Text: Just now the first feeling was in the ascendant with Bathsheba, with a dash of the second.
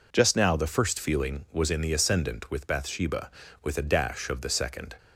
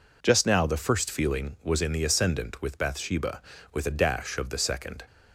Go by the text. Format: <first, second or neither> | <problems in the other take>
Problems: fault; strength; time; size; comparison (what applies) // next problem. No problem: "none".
neither | none